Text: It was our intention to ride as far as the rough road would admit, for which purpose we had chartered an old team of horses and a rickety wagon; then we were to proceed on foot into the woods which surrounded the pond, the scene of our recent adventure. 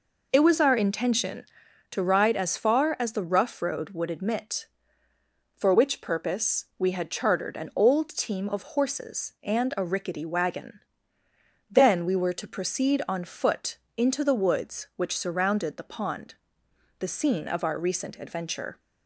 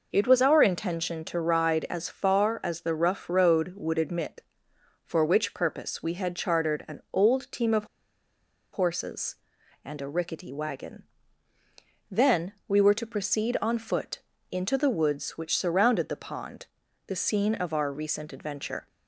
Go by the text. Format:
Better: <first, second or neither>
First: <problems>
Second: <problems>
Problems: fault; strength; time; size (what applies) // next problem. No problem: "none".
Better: first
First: pauses between "foot" and "into"; slight; at 13.7 s; 0.18 s long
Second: pauses between "of" and "horses"; noticeable; at 7.8 s; 0.88 s long // pauses between "foot" and "into"; slight; at 14.1 s; 0.30 s long